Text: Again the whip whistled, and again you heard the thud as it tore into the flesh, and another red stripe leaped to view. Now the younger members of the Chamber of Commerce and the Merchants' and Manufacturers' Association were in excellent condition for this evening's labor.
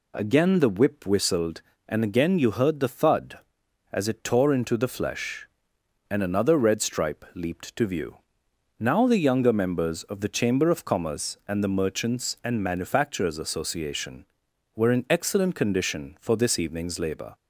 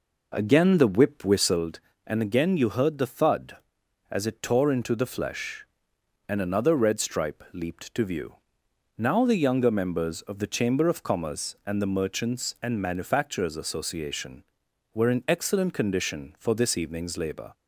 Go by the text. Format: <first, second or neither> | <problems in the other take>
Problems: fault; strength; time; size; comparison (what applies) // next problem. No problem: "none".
first | starts louder than the rest; noticeable; until 1.6 s; 4.5 dB